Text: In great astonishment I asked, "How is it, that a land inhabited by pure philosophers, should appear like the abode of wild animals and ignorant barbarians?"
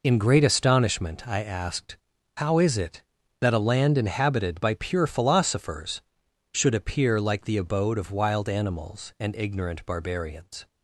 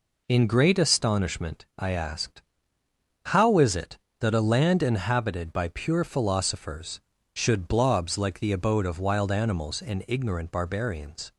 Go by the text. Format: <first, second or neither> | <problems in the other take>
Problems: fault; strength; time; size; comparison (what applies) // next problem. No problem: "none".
first | says "blobs" for "appear"; at 7.6 s